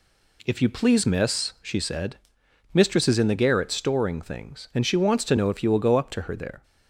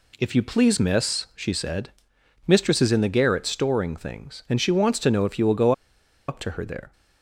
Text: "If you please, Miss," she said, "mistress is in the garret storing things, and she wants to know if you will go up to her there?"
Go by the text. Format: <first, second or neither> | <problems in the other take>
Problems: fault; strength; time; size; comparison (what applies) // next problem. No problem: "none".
first | pauses between "go" and "up"; noticeable; at 5.7 s; 0.56 s long